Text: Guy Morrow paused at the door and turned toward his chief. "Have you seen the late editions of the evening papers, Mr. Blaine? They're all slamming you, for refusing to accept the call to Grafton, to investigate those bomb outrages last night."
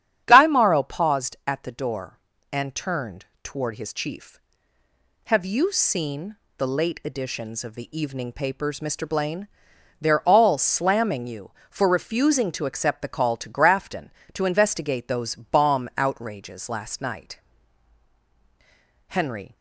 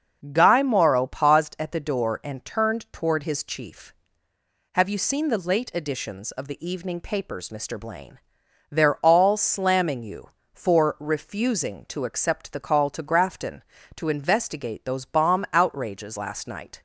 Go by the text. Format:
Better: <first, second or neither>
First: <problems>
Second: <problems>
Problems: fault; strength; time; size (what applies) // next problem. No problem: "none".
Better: second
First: starts louder than the rest; strong; until 1.2 s; 9.5 dB // pauses between "turned" and "toward"; slight; at 3.2 s; 0.18 s long // pauses between "seen" and "the"; slight; at 6.3 s; 0.18 s long // goes on to say "Henry"; slight; from 19.0 s on; 0.48 s long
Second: starts louder than the rest; strong; until 1.3 s; 7.5 dB